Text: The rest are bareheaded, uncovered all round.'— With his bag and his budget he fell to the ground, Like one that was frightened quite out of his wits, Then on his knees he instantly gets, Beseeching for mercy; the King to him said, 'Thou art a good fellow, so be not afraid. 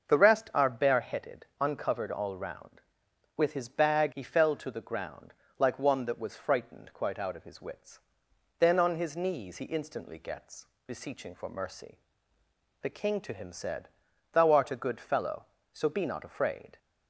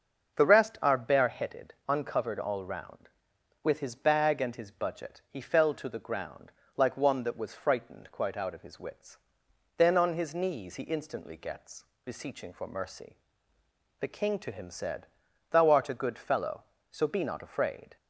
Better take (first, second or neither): second